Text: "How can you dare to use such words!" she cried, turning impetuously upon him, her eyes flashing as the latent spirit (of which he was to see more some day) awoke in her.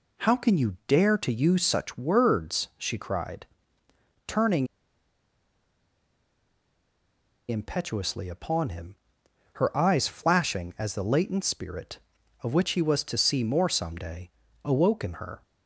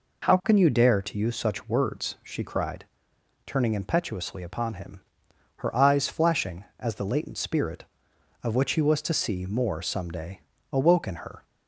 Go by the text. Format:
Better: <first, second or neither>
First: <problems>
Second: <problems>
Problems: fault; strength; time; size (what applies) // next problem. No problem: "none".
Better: second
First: pauses between "turning" and "impetuously"; strong; at 4.6 s; 2.8 s long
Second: none